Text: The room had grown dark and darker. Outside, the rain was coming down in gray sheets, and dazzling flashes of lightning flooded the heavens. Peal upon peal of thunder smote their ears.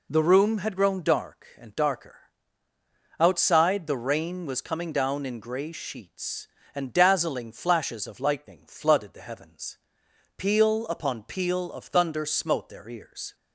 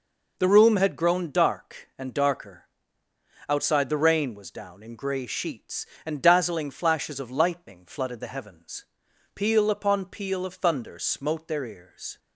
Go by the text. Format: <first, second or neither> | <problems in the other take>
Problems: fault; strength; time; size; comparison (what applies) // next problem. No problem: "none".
first | skips "coming"; at 4.5 s